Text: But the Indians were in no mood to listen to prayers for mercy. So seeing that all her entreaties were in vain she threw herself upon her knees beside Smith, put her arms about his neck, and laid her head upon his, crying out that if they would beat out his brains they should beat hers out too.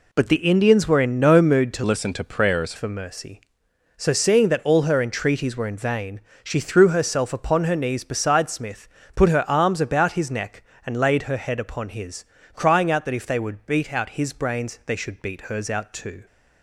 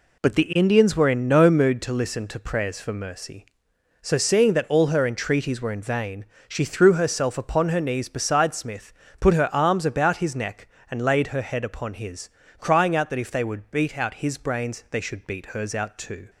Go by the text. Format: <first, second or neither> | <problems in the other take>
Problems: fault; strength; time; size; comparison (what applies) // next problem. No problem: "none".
second | changes voice from "listen" to "prayers"; from 1.8 to 2.7 s; 0.9 s long // pauses between "vain" and "she"; slight; at 6.2 s; 0.22 s long; slight in the second